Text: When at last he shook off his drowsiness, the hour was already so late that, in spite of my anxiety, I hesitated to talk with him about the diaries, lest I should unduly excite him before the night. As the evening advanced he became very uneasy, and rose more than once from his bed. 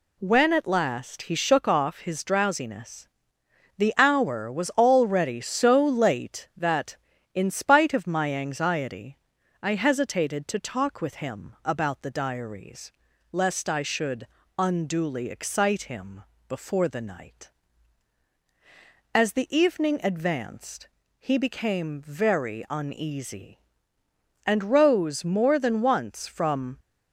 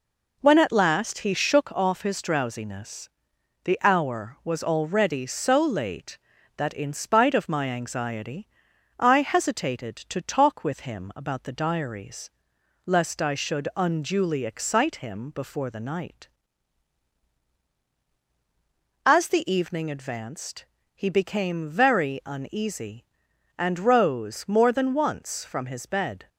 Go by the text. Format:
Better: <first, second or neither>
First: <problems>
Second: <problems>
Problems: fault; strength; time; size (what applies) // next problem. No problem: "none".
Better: second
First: pauses between "should" and "unduly"; slight; at 14.2 s; 0.30 s long // pauses between "him" and "before"; slight; at 16.2 s; 0.26 s long // pauses between "advanced" and "he"; slight; at 20.8 s; 0.32 s long // stops before "his bed"; at 26.7 s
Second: pauses between "advanced" and "he"; slight; at 20.6 s; 0.30 s long